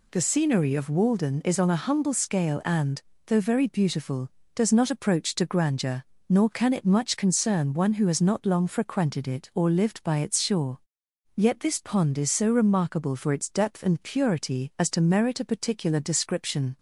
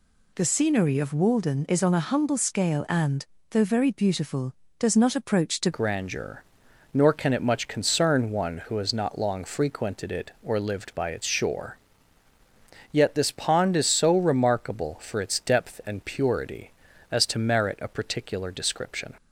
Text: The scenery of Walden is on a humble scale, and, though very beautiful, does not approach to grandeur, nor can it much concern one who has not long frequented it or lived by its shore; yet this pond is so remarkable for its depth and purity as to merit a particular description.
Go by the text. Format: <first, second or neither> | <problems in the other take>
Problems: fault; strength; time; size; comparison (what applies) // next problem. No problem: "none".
first | changes voice at "grandeur"; from 5.7 s on; 13.4 s long